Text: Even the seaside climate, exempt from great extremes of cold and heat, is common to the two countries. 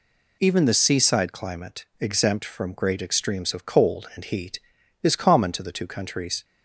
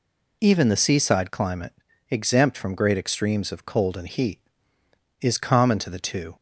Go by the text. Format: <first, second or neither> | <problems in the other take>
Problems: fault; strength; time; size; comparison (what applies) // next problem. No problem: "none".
first | stops before "countries"; at 6.3 s